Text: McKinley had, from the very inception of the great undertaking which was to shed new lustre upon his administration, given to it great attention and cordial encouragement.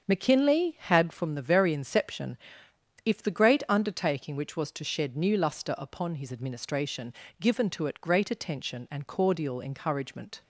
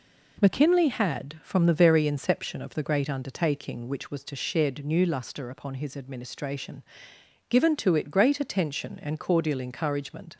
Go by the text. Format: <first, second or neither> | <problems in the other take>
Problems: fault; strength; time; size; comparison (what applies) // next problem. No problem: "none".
second | starts louder than the rest; strong; until 1.0 s; 7.5 dB // says "if" for "of"; at 3.0 s